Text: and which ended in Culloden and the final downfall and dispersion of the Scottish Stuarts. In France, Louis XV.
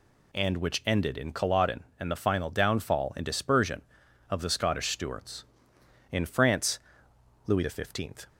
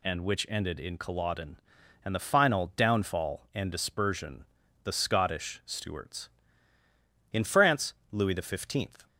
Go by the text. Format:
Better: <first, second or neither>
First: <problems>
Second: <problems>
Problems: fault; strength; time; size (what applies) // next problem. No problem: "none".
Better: first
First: none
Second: skips "of"; at 4.6 s